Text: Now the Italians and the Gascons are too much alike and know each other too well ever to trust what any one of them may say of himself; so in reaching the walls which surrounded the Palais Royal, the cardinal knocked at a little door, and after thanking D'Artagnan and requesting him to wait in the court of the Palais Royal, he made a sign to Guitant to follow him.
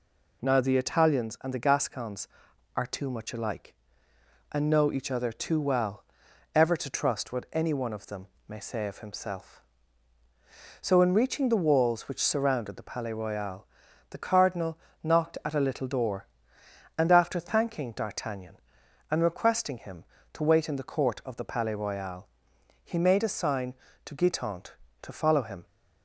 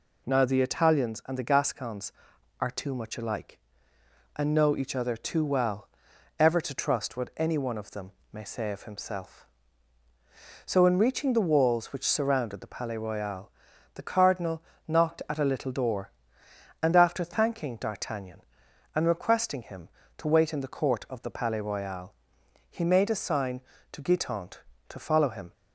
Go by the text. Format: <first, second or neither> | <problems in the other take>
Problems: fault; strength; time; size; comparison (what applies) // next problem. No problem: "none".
neither | pauses between "well" and "ever"; noticeable; the same in both // pauses between "them" and "may"; slight; the same in both // pauses between "cardinal" and "knocked"; slight; the same in both